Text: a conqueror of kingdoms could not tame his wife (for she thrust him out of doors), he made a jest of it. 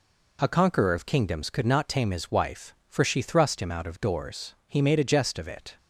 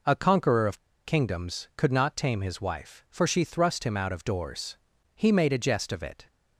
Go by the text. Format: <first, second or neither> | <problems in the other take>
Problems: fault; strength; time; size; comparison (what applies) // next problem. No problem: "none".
first | pauses between "of" and "kingdoms"; slight; at 0.7 s; 0.26 s long